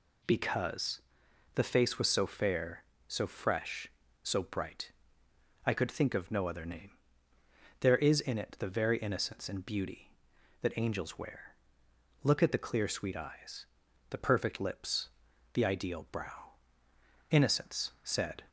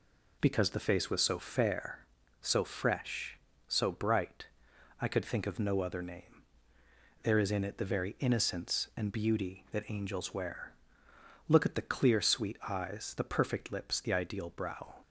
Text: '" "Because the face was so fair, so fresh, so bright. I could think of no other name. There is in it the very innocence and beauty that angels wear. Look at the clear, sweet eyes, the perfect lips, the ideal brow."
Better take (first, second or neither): second